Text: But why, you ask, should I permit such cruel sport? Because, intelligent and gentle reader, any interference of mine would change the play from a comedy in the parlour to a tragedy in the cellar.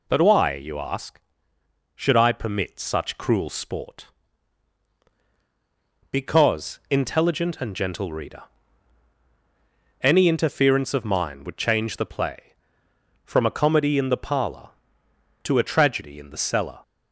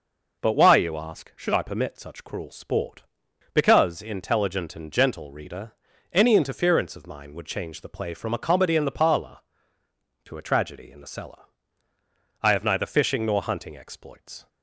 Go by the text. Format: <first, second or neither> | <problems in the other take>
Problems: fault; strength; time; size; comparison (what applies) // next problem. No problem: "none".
first | goes on to say "I have neither fishing nor hunting exploits"; strong; from 12.4 s on; 2.0 s long